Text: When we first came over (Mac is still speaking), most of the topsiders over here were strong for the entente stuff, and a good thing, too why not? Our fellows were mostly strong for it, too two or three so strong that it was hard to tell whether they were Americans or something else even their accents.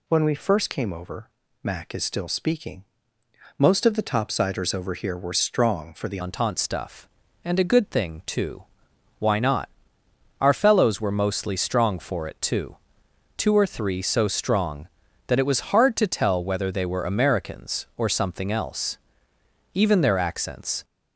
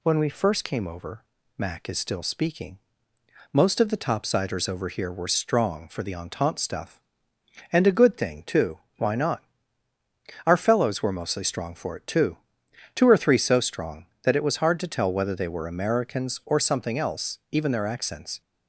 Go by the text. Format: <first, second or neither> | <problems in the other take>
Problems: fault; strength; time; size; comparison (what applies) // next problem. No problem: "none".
second | changes voice at "entente"; from 6.2 s on; 14.6 s long // pauses between "too" and "why"; noticeable; at 8.6 s; 0.54 s long; slight in the second // pauses between "too" and "two"; noticeable; at 12.7 s; 0.62 s long; noticeable in the second // pauses between "else" and "even"; noticeable; at 18.9 s; 0.74 s long